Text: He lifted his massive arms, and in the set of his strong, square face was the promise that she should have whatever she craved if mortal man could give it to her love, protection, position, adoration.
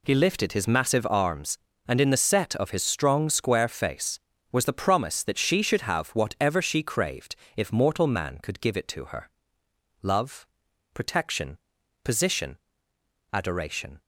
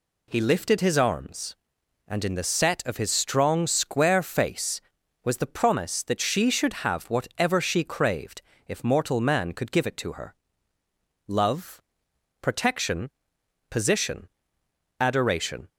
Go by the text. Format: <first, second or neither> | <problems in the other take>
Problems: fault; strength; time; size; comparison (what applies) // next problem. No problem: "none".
first | skips "massive"; at 0.9 s // pauses between "craved" and "if"; slight; at 8.4 s; 0.24 s long; slight in the first // pauses between "her" and "love"; noticeable; at 10.3 s; 0.92 s long; noticeable in the first